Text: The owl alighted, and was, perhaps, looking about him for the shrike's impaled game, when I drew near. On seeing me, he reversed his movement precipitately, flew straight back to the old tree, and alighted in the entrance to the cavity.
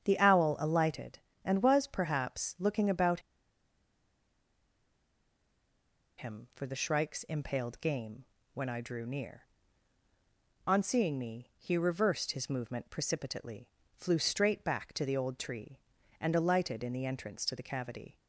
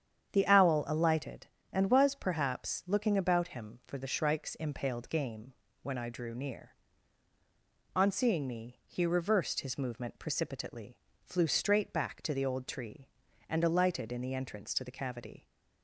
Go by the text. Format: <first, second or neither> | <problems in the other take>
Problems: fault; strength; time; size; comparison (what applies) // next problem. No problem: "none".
second | starts louder than the rest; strong; until 1.0 s; 8.5 dB; strong in the second // pauses between "about" and "him"; strong; at 3.2 s; 2.9 s long